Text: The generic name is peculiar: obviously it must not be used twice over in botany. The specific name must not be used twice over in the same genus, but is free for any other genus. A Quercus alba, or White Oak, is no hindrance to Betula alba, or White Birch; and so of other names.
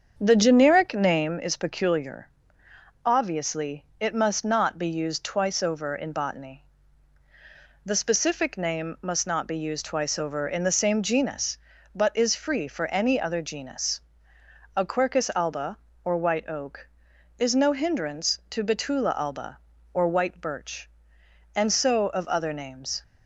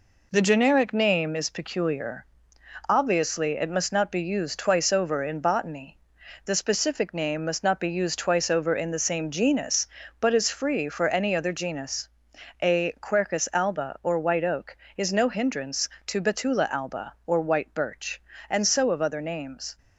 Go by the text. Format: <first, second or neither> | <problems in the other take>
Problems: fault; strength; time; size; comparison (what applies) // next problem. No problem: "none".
second | starts louder than the rest; strong; until 1.5 s; 7.5 dB // pauses between "obviously" and "it"; slight; at 3.8 s; 0.16 s long